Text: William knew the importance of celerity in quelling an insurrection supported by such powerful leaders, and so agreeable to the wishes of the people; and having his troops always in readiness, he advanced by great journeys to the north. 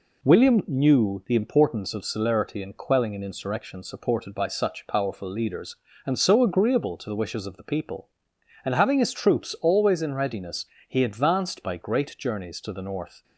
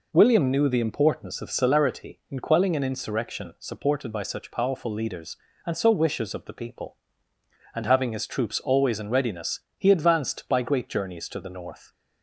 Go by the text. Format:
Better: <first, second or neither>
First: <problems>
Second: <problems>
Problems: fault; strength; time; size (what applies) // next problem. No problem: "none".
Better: first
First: none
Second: skips "agreeable to the"; at 5.9 s